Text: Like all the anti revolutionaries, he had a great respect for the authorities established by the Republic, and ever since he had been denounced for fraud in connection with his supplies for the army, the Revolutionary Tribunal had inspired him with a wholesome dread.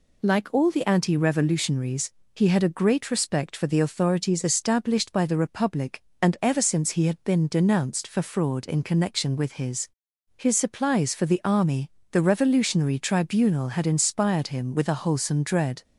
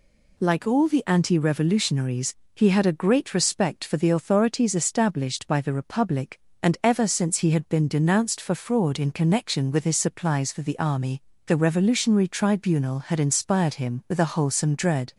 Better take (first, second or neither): second